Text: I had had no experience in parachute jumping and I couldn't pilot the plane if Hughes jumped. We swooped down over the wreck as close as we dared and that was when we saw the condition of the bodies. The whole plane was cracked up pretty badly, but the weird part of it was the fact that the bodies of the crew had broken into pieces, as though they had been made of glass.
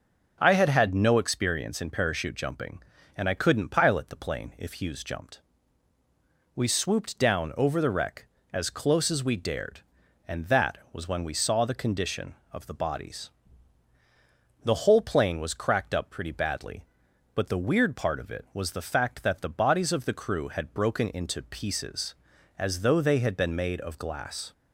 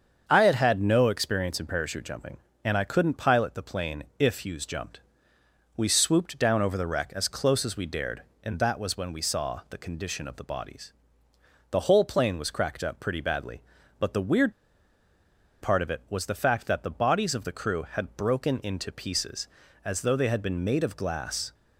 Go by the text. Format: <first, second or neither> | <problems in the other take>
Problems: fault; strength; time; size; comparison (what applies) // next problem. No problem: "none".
first | starts louder than the rest; until 1.2 s; 7 dB // pauses between "weird" and "part"; at 14.5 s; 1.1 s long